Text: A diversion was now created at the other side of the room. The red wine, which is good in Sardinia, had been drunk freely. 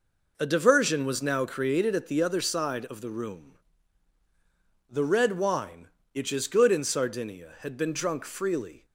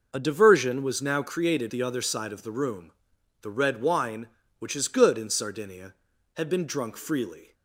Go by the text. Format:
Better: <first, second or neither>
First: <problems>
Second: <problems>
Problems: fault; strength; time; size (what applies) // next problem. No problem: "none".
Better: first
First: none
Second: skips "at"; at 1.7 s